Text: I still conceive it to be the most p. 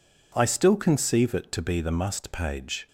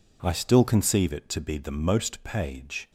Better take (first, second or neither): second